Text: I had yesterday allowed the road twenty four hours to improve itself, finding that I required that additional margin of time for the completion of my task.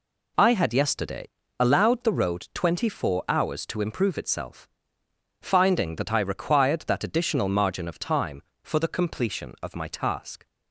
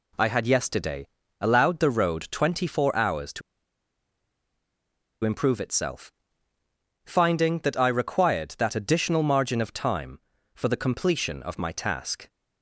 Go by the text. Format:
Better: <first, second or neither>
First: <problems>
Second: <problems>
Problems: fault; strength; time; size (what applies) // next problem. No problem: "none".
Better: first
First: pauses between "yesterday" and "allowed"; slight; at 1.2 s; 0.32 s long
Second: pauses between "yesterday" and "allowed"; slight; at 1.0 s; 0.34 s long // pauses between "to" and "improve"; strong; at 3.4 s; 1.8 s long